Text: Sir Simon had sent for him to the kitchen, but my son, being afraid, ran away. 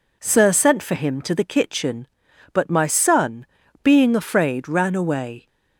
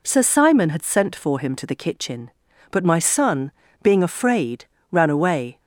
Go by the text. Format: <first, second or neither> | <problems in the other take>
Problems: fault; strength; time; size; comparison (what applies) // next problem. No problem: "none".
second | skips "Simon had"; at 0.5 s